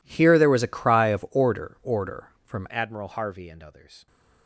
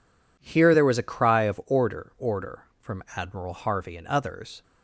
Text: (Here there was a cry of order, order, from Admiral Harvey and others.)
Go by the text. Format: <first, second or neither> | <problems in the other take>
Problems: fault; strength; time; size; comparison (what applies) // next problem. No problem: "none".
second | changes voice at "Admiral"; from 2.7 s on; 1.3 s long